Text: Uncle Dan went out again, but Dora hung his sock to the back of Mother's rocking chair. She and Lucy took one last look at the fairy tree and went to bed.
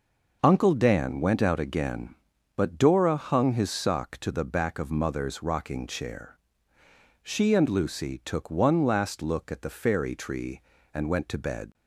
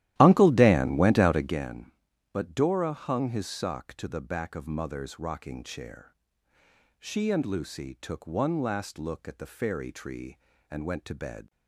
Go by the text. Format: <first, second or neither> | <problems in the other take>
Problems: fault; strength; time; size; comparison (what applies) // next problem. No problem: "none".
first | starts louder than the rest; strong; until 1.6 s; 14 dB